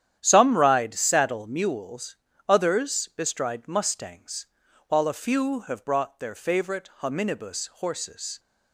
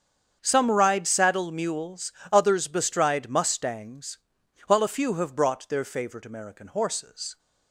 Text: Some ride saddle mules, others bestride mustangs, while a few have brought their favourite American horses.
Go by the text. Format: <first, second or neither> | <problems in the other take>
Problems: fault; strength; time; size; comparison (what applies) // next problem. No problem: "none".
second | starts louder than the rest; strong; until 1.2 s; 10 dB; strong in the second // says "Hominibus" for "American"; at 7.0 s